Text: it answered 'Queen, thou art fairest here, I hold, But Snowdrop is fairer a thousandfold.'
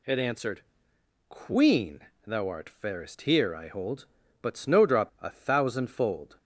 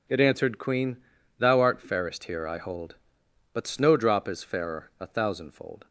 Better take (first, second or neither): second